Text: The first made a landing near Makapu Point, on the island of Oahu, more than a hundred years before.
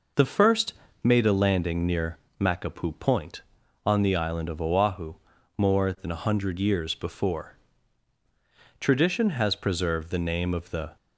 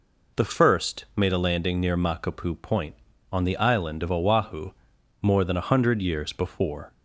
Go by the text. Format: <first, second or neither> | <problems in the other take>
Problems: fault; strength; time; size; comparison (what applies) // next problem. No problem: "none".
second | pauses between "first" and "made"; slight; at 0.7 s; 0.32 s long // pauses between "near" and "Makapu"; slight; at 2.1 s; 0.20 s long // goes on to say "Tradition has preserved the name of the"; strong; from 8.7 s on; 2.1 s long